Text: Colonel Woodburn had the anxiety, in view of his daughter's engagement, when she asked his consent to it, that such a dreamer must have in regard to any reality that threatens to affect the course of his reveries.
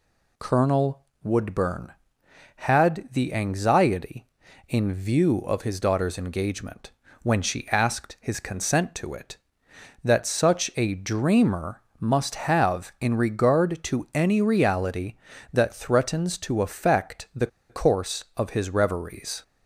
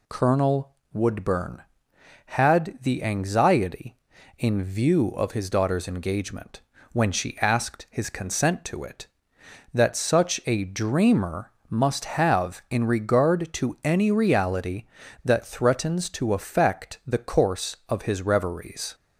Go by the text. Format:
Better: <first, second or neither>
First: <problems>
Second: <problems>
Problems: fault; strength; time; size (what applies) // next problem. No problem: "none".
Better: second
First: pauses between "Colonel" and "Woodburn"; slight; at 1.0 s; 0.18 s long // pauses between "dreamer" and "must"; slight; at 11.8 s; 0.20 s long // pauses between "the" and "course"; slight; at 17.4 s; 0.22 s long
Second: pauses between "Colonel" and "Woodburn"; slight; at 0.7 s; 0.18 s long // pauses between "dreamer" and "must"; slight; at 11.5 s; 0.20 s long